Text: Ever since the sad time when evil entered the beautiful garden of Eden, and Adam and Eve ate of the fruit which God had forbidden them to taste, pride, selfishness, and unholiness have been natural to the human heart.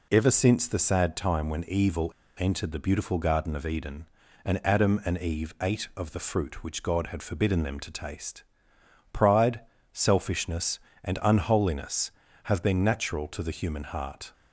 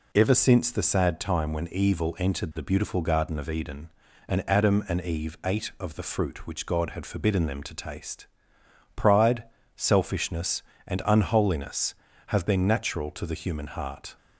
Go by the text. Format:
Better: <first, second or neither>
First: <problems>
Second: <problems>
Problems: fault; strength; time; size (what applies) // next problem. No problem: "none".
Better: second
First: pauses between "evil" and "entered"; slight; at 2.1 s; 0.26 s long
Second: none